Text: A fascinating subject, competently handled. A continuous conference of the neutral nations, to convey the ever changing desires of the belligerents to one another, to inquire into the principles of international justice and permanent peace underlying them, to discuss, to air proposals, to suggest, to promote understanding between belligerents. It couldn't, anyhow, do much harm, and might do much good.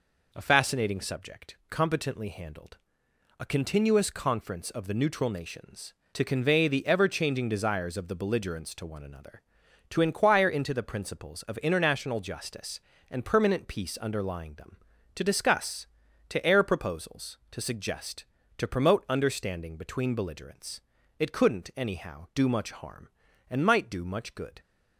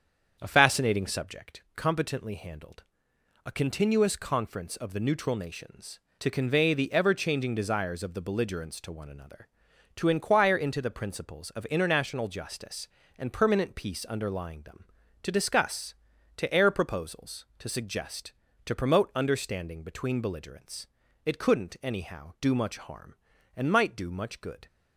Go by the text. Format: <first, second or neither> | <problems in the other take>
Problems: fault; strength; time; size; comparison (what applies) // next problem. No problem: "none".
first | starts louder than the rest; strong; until 1.5 s; 7.5 dB